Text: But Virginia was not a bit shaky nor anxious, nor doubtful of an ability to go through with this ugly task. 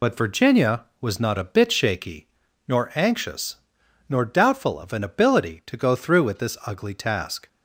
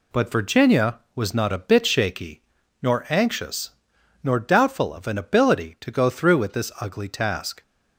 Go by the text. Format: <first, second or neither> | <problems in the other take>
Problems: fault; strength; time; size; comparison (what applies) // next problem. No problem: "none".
second | loses the start of "But"; at 0.0 s; 45 ms // pauses between "shaky" and "nor"; at 2.2 s; 0.42 s long; also in the second